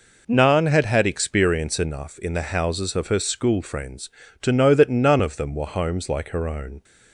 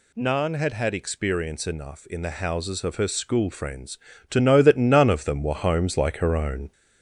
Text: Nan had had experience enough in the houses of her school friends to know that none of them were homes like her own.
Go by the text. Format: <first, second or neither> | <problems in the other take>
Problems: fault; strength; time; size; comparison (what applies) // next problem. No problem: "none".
first | gets louder; slight; throughout; 2.5 dB